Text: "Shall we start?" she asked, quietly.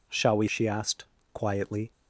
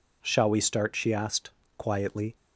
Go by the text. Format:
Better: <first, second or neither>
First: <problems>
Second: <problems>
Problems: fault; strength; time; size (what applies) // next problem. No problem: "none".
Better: second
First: skips "start"; at 0.4 s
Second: none